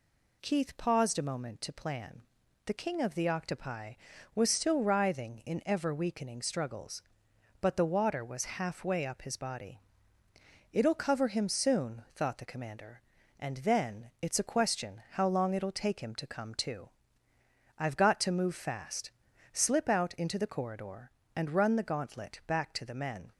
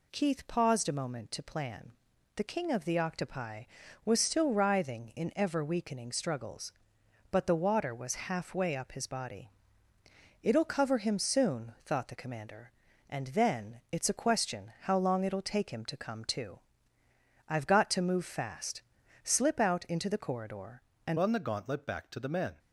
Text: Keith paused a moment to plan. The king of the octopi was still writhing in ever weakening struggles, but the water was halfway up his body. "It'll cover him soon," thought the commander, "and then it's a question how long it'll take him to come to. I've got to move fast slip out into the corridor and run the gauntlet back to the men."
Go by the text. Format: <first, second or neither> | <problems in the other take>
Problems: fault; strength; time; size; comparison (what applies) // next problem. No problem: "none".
first | pauses between "fast" and "slip"; at 18.8 s; 0.42 s long; also in the first // changes voice at "run"; from 21.1 s on; 1.4 s long